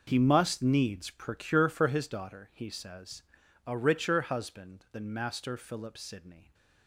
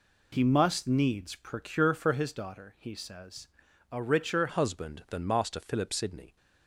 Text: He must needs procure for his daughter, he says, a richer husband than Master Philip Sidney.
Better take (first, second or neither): first